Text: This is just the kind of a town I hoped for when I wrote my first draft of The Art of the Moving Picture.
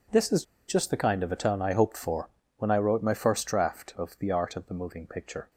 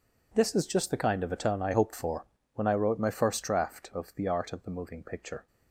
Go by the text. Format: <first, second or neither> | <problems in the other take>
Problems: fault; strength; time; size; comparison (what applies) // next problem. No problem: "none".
second | pauses between "is" and "just"; slight; at 0.4 s; 0.24 s long // pauses between "for" and "when"; slight; at 2.3 s; 0.26 s long; slight in the second